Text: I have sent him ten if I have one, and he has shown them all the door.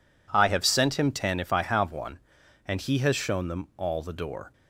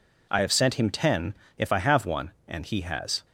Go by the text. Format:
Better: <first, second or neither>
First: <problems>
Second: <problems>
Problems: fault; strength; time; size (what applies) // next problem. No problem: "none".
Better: first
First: none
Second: pauses between "ten" and "if"; slight; at 1.3 s; 0.22 s long // stops before "shown them all the door"; at 3.2 s